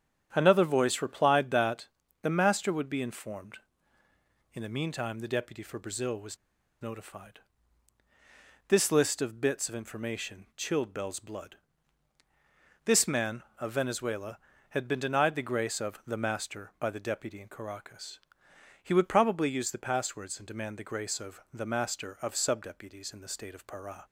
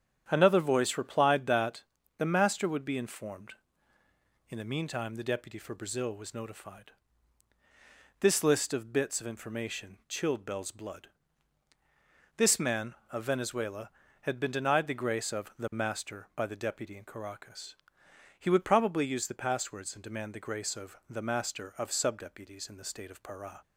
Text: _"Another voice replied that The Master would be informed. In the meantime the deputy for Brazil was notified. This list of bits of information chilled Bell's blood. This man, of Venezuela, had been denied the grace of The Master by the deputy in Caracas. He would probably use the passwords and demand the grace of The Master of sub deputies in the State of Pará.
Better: second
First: starts louder than the rest; strong; until 1.3 s; 9 dB // pauses between "that" and "The"; slight; at 1.8 s; 0.34 s long // pauses between "was" and "notified"; noticeable; at 6.3 s; 0.46 s long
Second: starts louder than the rest; strong; until 1.2 s; 9 dB // pauses between "that" and "The"; slight; at 1.8 s; 0.34 s long

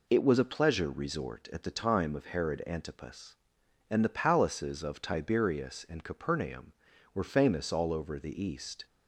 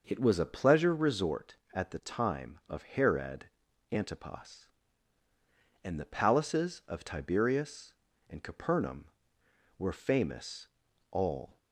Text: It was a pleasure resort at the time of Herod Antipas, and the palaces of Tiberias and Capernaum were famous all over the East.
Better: first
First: none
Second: pauses between "Herod" and "Antipas"; at 3.4 s; 0.44 s long // pauses between "famous" and "all"; at 10.6 s; 0.44 s long // stops before "over the East"; at 11.5 s

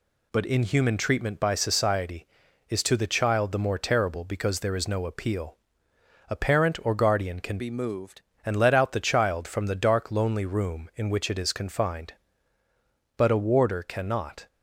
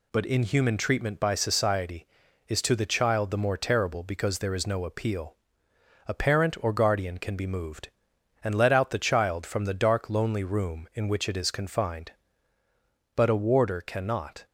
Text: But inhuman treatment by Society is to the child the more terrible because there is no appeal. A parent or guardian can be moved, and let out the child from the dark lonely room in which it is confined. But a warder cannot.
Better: second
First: changes voice from "be" to "moved"; from 7.5 to 8.2 s; 0.7 s long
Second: none

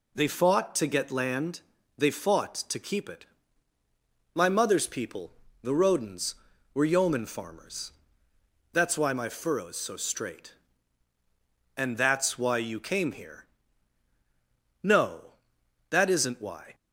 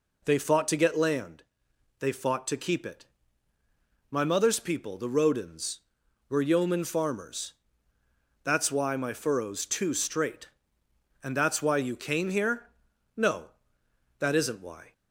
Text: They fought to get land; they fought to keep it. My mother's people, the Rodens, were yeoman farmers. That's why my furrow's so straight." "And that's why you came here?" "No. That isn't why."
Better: first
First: none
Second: says "too" for "so"; at 9.6 s

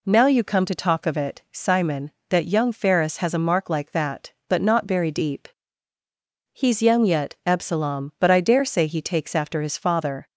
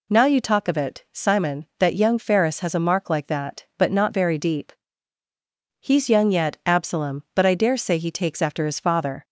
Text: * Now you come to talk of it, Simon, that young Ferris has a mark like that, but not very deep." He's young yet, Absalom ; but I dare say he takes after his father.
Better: first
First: none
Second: skips "come to"; at 0.4 s

